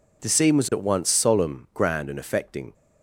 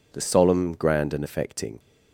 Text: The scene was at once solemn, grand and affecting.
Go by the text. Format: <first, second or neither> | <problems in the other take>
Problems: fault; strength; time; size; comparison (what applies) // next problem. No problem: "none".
first | skips "scene was at once"; at 0.2 s